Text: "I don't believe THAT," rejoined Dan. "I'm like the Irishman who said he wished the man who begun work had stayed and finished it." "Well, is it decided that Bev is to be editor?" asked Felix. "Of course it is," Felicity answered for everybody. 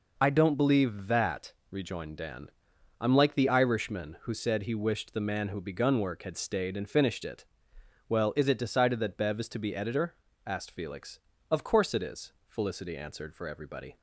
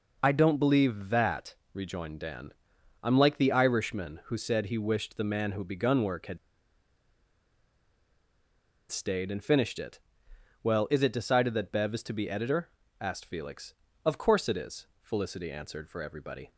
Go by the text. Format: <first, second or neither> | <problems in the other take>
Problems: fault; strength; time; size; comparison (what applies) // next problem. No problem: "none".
first | pauses between "had" and "stayed"; strong; at 6.3 s; 2.5 s long